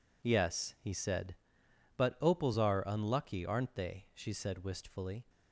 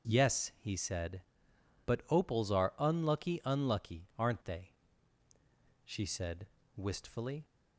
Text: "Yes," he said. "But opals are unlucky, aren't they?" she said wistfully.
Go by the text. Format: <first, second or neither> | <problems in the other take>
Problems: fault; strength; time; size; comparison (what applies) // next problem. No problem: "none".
first | says "unlucky" twice; at 3.4 s // pauses between "said" and "wistfully"; slight; at 6.4 s; 0.30 s long